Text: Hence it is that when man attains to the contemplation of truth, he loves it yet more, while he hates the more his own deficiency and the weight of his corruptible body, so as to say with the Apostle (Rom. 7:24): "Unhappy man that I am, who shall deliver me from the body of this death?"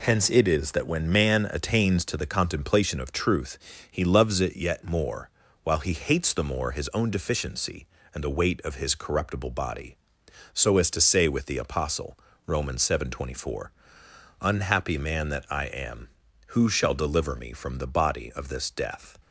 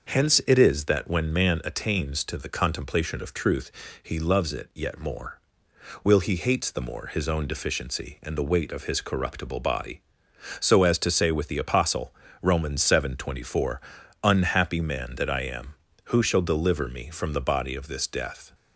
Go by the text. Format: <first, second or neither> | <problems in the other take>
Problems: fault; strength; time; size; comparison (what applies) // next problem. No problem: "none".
first | starts louder than the rest; until 1.1 s; 6 dB // says "will" for "while"; at 6.0 s